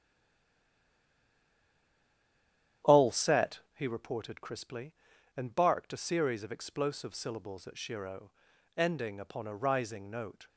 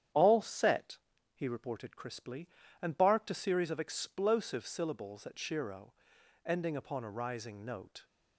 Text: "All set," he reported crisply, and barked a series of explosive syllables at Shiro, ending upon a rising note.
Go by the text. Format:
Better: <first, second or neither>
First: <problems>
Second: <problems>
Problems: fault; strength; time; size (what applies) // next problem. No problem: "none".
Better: second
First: stays silent before the first word; strong; until 2.8 s; 2.8 s long // starts louder than the rest; strong; until 4.0 s; 10.5 dB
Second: starts louder than the rest; strong; until 1.4 s; 9.5 dB